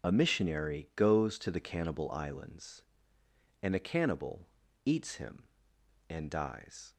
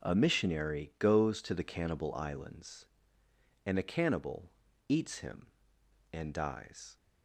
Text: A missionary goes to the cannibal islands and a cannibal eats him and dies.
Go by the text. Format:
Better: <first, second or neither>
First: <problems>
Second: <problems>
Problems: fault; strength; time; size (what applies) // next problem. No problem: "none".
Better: second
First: loses the start of "A"; at 0.0 s; 50 ms // starts louder than the rest; until 1.1 s; 6.5 dB // pauses between "cannibal" and "eats"; at 4.4 s; 0.40 s long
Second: pauses between "cannibal" and "eats"; at 4.4 s; 0.40 s long